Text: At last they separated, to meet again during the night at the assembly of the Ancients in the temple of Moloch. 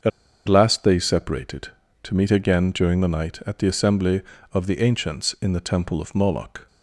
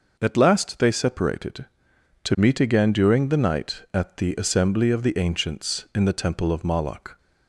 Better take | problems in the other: second | starts louder than the rest; until 1.4 s; 7 dB // pauses between "At" and "last"; at 0.1 s; 0.38 s long

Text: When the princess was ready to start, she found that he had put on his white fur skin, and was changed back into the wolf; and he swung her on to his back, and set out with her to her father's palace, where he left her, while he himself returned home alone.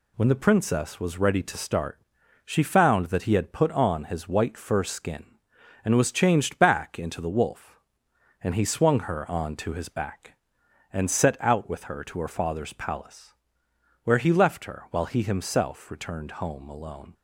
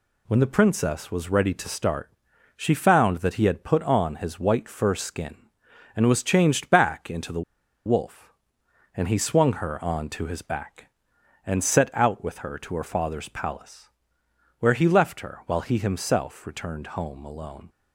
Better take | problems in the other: first | pauses between "the" and "wolf"; at 7.4 s; 0.43 s long

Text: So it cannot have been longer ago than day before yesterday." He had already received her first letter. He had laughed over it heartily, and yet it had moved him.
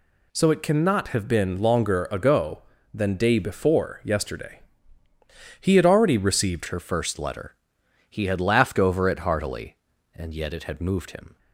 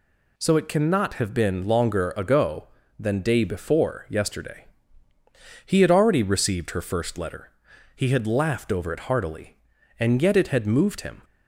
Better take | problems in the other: second | changes voice at "her"; from 6.6 s on; 4.7 s long

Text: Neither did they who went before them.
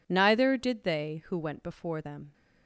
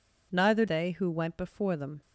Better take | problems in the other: first | skips "did"; at 0.6 s

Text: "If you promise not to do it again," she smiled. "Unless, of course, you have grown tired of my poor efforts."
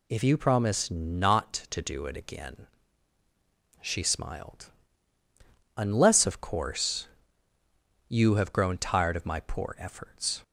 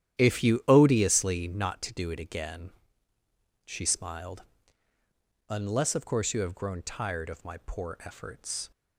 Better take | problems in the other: first | starts louder than the rest; strong; until 1.2 s; 11 dB // says "odiously" for "promise"; at 0.6 s

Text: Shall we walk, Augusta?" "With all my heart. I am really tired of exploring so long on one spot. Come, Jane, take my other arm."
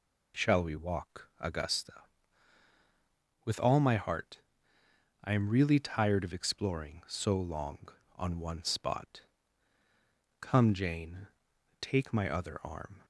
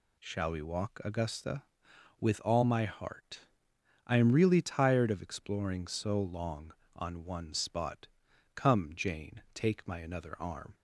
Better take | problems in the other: first | says "another" for "other"; at 9.9 s

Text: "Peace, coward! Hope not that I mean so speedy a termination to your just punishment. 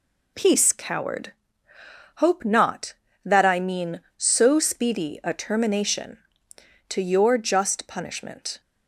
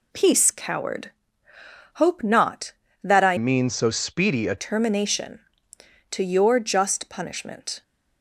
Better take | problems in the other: first | changes voice from "mean" to "a"; from 3.3 to 4.5 s; 1.2 s long

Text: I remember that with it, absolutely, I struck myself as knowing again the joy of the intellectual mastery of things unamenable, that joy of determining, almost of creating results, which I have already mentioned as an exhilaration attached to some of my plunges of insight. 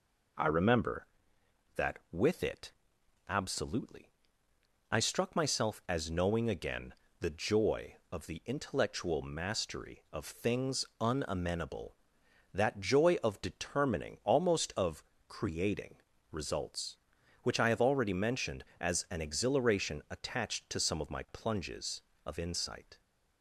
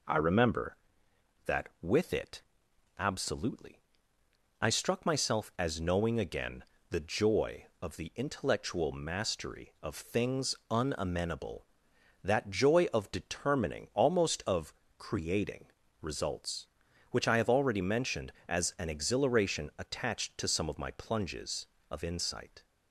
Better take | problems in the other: neither | pauses between "again" and "the"; slight; the same in both // pauses between "of" and "creating"; slight; the same in both // pauses between "creating" and "results"; the same in both

